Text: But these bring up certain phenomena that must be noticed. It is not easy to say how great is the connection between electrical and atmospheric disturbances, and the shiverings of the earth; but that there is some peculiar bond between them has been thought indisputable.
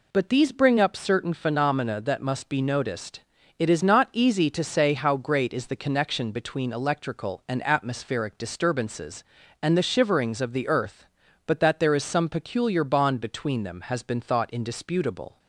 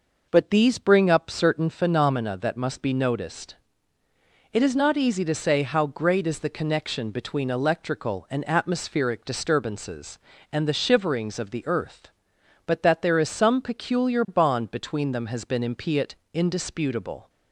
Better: first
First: none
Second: says "impiet" for "thought"; at 15.6 s

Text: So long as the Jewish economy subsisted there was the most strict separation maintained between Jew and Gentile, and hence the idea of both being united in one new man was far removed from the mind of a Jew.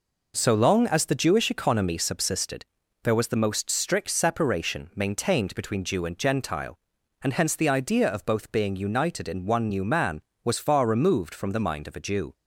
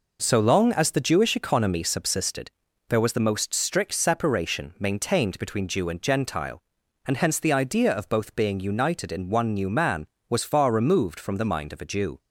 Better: neither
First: pauses between "subsisted" and "there"; at 2.6 s; 0.40 s long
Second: pauses between "subsisted" and "there"; at 2.5 s; 0.40 s long

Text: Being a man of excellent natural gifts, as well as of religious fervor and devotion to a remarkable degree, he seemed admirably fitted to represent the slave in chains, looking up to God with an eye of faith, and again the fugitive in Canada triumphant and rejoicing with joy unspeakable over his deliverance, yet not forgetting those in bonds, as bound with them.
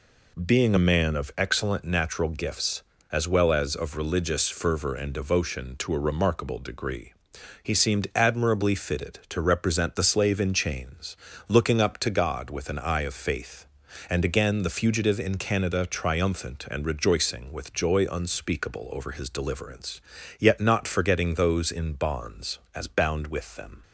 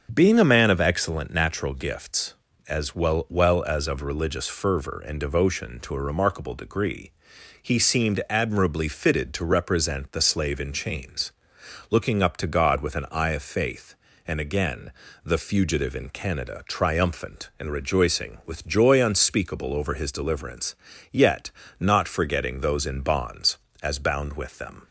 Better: first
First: none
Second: starts louder than the rest; until 1.1 s; 6.5 dB // says "well" twice; at 3.2 s // pauses between "again" and "the"; slight; at 14.9 s; 0.32 s long // pauses between "yet" and "not"; slight; at 21.5 s; 0.28 s long

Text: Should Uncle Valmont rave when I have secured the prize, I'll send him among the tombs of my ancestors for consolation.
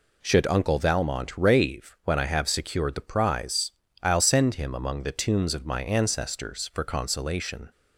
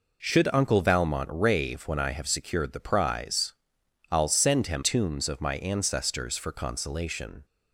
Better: first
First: none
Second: skips "among the"; at 4.8 s

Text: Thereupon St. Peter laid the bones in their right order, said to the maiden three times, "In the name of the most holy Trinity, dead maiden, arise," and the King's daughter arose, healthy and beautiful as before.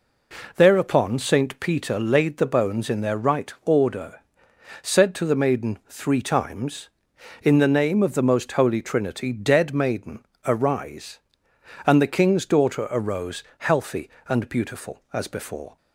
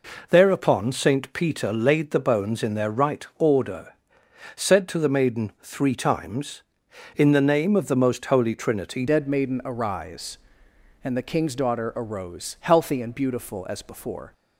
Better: first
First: none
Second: changes voice at "dead"; from 9.0 s on; 5.3 s long

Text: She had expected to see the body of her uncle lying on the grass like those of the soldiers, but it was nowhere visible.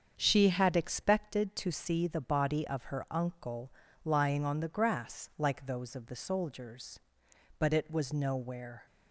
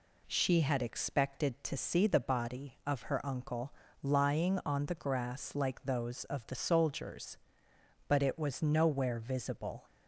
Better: second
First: starts louder than the rest; strong; until 1.1 s; 7 dB // pauses between "uncle" and "lying"; slight; at 3.7 s; 0.32 s long // stops before "visible"; at 8.8 s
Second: pauses between "uncle" and "lying"; slight; at 3.7 s; 0.28 s long

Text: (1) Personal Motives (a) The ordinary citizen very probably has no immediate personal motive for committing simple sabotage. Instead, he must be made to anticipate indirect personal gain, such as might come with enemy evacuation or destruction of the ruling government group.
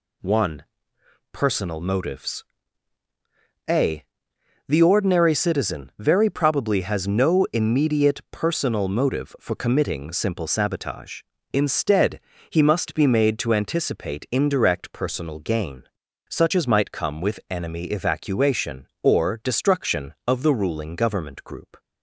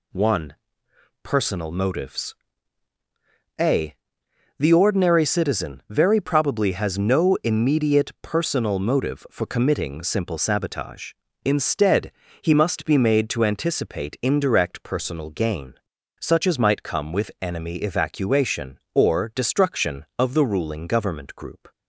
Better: neither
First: pauses between "Motives" and "a"; at 2.4 s; 1.2 s long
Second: pauses between "Motives" and "a"; at 2.3 s; 1.2 s long

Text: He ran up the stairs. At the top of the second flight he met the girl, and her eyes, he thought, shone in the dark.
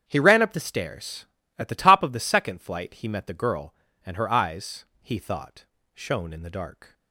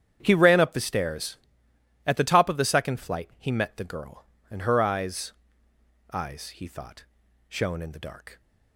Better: first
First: starts louder than the rest; strong; until 1.0 s; 8 dB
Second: starts louder than the rest; strong; until 1.2 s; 9 dB // says "eyes" twice; at 6.1 s

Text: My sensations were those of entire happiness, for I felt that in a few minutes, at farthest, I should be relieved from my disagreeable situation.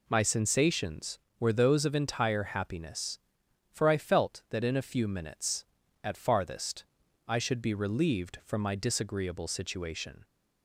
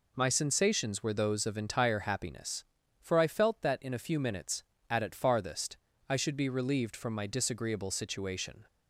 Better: first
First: none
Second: says "at" twice; at 5.0 s

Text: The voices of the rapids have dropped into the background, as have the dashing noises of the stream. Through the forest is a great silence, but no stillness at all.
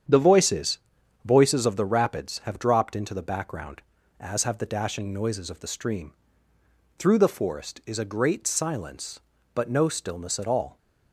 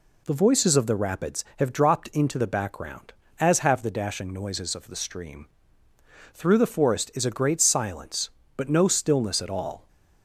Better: second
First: starts louder than the rest; strong; until 1.5 s; 8.5 dB // says "voices" twice; at 1.2 s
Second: none

